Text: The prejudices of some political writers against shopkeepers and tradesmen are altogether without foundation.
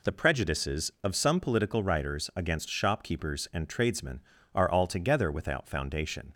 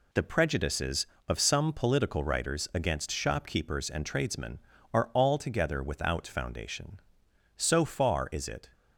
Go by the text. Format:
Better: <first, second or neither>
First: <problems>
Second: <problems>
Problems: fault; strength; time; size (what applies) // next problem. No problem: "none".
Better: first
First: none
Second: goes on to say "So far is it"; noticeable; from 7.6 s on; 1.1 s long